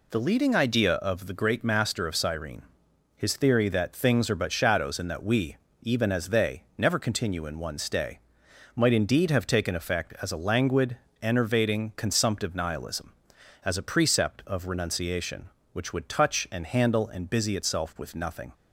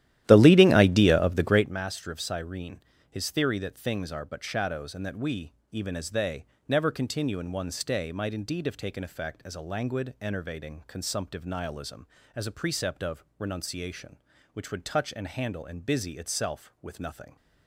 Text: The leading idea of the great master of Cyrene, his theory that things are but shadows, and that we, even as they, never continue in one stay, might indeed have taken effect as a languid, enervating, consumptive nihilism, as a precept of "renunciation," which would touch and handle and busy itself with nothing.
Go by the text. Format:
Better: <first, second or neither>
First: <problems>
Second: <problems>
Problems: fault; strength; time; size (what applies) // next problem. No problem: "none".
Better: first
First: none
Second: starts louder than the rest; strong; until 1.7 s; 13 dB // pauses between "of" and "renunciation"; slight; at 13.2 s; 0.16 s long